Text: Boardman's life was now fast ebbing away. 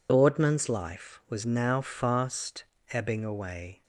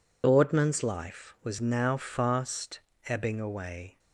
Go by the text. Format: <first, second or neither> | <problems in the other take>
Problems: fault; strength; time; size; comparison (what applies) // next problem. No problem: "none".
neither | pauses between "fast" and "ebbing"; slight; the same in both